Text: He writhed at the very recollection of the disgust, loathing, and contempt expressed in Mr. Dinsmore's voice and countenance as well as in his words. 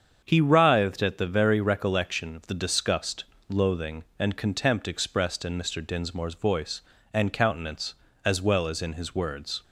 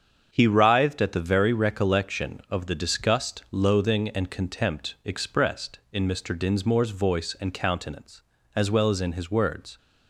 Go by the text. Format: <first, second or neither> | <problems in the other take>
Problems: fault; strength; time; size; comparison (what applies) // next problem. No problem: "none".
neither | starts louder than the rest; strong; the same in both